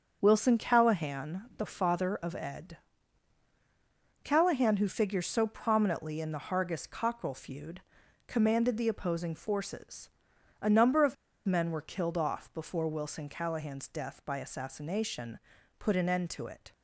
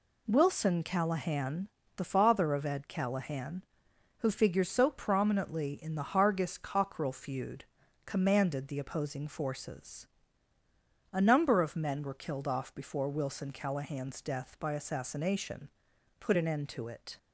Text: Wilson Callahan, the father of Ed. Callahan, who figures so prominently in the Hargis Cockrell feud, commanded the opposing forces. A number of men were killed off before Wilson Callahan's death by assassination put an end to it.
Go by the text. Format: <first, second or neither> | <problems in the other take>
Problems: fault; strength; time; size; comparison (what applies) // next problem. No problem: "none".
second | starts louder than the rest; until 1.2 s; 7 dB // pauses between "of" and "men"; slight; at 11.1 s; 0.30 s long // pauses between "assassination" and "put"; at 15.3 s; 0.40 s long; noticeable in the second